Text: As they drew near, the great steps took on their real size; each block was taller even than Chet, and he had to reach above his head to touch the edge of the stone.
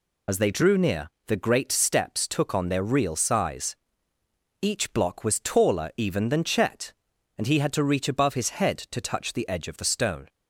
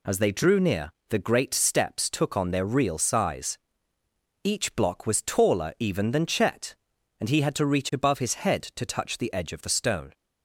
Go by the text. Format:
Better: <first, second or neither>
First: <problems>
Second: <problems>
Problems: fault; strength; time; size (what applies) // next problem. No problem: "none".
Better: second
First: loses the start of "As"; at 0.2 s; 40 ms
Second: none